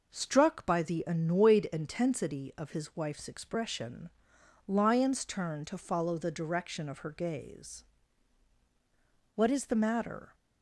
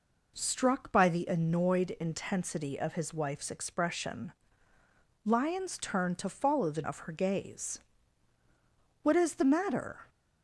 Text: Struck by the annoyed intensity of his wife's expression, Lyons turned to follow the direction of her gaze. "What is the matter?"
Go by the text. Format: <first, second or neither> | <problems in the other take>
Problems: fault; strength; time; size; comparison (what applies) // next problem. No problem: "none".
first | skips "direction"; at 6.8 s